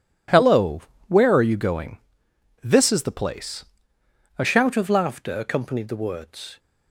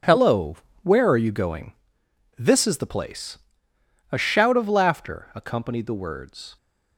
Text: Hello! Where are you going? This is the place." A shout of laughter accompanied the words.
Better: second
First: changes voice at "shout"; from 4.4 s on; 2.1 s long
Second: none

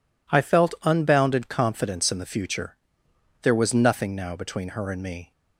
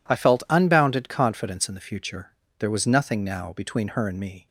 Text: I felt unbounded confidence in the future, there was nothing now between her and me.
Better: neither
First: none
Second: none

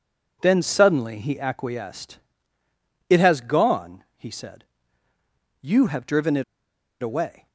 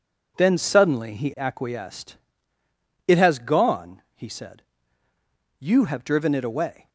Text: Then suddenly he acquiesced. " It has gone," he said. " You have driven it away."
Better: second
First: starts louder than the rest; strong; until 1.4 s; 8.5 dB // pauses between "it" and "away"; noticeable; at 6.4 s; 0.58 s long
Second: starts louder than the rest; strong; until 1.3 s; 8.5 dB

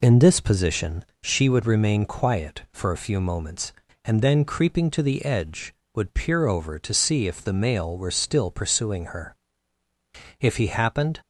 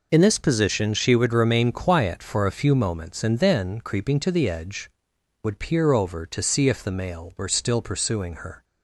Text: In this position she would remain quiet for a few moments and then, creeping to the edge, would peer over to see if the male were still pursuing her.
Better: second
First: pauses between "position" and "she"; slight; at 1.0 s; 0.18 s long // goes on to say "If he happened"; noticeable; from 10.4 s on; 0.80 s long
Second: none

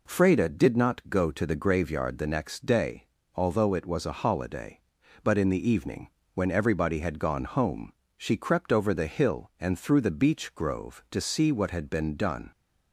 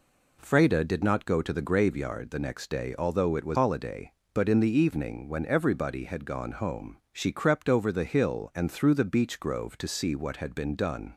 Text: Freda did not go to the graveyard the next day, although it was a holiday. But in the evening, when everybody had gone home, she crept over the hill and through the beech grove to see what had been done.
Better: first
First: none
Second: skips "a"; at 3.5 s

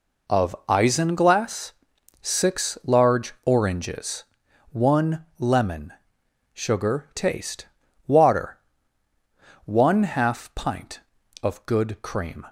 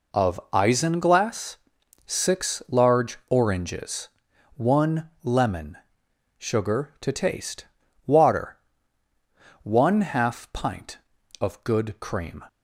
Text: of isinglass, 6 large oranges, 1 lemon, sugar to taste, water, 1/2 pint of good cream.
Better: second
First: skips "to"; at 7.1 s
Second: none

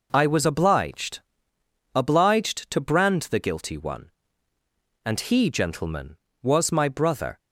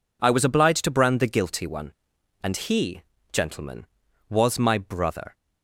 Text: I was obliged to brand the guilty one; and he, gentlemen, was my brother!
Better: second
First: says "obliged" twice; at 1.9 s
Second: none

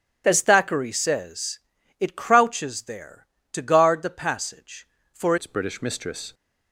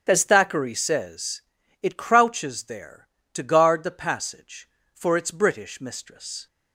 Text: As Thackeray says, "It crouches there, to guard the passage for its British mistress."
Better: second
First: starts louder than the rest; strong; until 1.2 s; 9 dB // changes voice at "its"; from 5.3 s on; 1.0 s long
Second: starts louder than the rest; strong; until 1.0 s; 8 dB

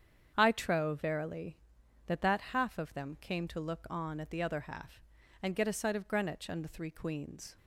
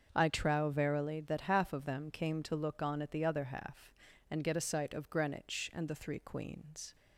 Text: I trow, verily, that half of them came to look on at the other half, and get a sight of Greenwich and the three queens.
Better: second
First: starts louder than the rest; strong; until 1.3 s; 8 dB // says "that" twice; at 2.2 s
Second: starts louder than the rest; until 1.1 s; 6.5 dB

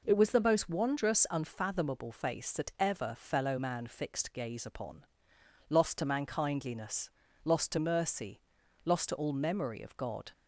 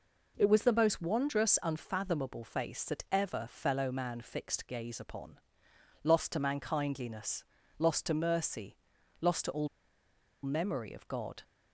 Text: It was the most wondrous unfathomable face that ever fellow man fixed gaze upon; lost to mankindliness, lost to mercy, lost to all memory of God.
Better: first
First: none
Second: pauses between "all" and "memory"; noticeable; at 9.6 s; 0.77 s long

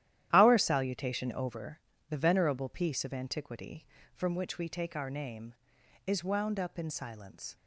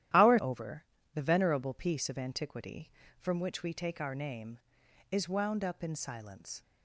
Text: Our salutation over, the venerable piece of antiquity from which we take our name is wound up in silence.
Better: first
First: starts louder than the rest; strong; until 1.3 s; 12 dB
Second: starts louder than the rest; strong; until 1.4 s; 12 dB // skips "salutation"; at 0.3 s

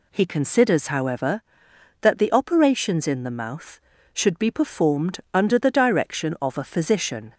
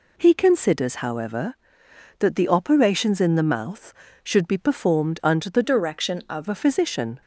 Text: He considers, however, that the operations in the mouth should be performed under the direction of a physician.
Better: first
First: none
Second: changes voice from "direction" to "of"; from 5.6 to 6.4 s; 0.8 s long

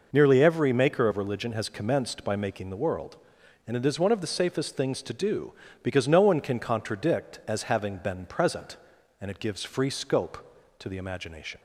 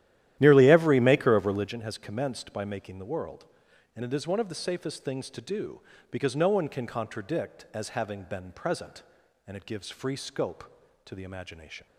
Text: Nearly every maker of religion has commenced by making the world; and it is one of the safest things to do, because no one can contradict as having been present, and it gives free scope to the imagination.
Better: first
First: none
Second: starts louder than the rest; strong; until 1.7 s; 12.5 dB

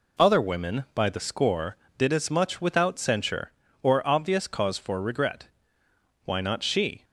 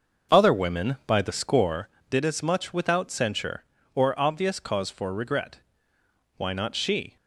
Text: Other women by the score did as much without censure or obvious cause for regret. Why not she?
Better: first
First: none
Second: starts louder than the rest; noticeable; until 1.8 s; 6 dB

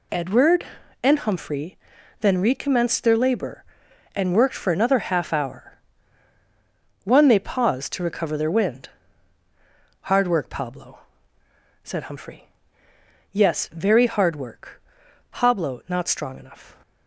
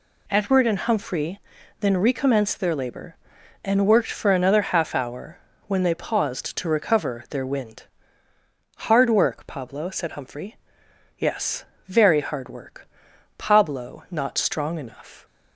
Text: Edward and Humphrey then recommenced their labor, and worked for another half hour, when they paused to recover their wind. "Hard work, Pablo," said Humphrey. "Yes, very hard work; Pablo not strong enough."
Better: second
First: pauses between "Humphrey" and "then"; at 1.7 s; 0.44 s long // says "one" for "when"; at 7.0 s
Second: pauses between "Humphrey" and "then"; at 1.3 s; 0.40 s long

